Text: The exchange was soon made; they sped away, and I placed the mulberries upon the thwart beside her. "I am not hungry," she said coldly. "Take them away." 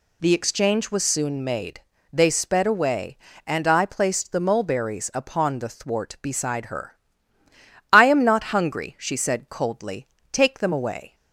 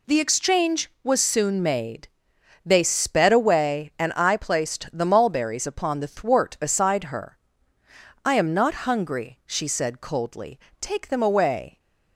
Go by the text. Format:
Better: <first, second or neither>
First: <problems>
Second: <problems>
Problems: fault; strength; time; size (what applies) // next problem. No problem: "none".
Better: neither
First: none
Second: none